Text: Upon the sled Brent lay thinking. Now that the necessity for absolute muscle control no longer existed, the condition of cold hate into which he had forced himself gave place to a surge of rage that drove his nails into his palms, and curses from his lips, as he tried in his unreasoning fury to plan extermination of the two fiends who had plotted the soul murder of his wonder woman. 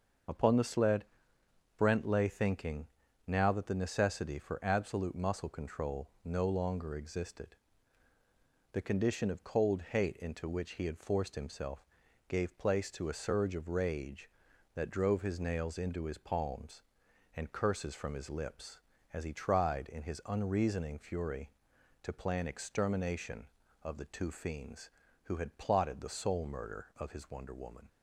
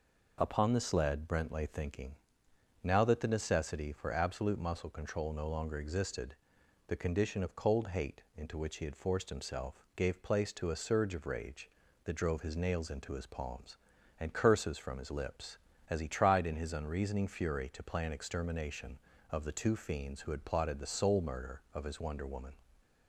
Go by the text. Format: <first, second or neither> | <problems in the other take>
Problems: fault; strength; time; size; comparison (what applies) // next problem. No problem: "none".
second | loses the start of "Upon"; at 0.2 s; 25 ms // starts louder than the rest; until 2.0 s; 6.5 dB // pauses between "sled" and "Brent"; noticeable; at 1.0 s; 0.72 s long // pauses between "control" and "no"; slight; at 6.0 s; 0.16 s long // pauses between "himself" and "gave"; at 11.8 s; 0.42 s long